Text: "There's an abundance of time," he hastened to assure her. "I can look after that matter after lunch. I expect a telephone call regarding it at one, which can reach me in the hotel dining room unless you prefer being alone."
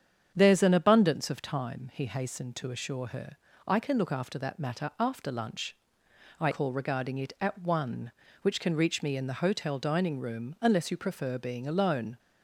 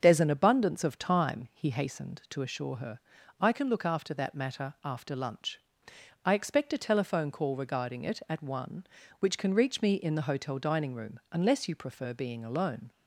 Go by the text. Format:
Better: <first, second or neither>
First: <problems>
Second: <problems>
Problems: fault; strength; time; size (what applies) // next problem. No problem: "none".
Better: second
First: starts louder than the rest; strong; until 1.3 s; 8 dB // skips "expect a telephone"; at 6.4 s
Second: starts louder than the rest; until 1.0 s; 7 dB